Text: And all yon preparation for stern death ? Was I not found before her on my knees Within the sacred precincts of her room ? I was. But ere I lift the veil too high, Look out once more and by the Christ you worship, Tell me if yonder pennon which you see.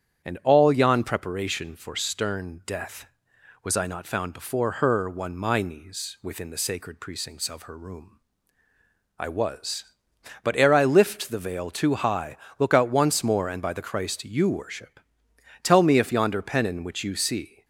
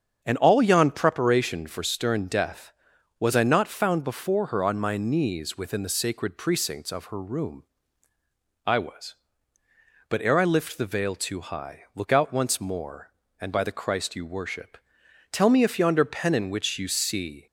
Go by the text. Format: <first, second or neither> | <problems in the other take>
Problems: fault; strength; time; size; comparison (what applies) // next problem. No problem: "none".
second | starts louder than the rest; strong; until 1.2 s; 9 dB; strong in the second // says "one" for "on"; at 5.0 s